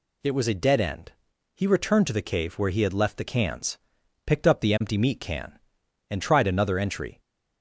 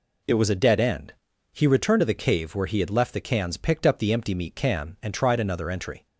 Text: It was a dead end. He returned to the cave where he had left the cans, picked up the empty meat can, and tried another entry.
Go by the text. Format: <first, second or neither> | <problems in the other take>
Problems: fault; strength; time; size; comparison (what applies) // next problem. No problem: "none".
neither | none